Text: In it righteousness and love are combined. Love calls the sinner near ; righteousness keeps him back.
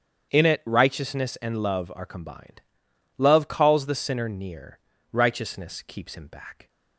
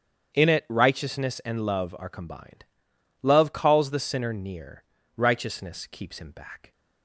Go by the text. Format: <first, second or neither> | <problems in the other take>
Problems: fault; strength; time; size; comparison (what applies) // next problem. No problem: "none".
neither | starts louder than the rest; strong; the same in both